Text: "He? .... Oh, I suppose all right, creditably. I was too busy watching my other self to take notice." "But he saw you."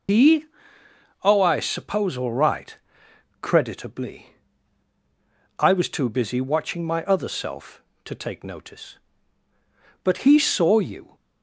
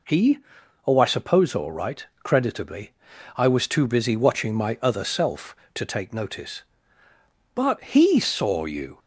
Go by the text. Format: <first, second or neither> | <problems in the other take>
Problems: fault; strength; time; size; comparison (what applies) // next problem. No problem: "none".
second | loses the start of "He"; at 0.0 s; 100 ms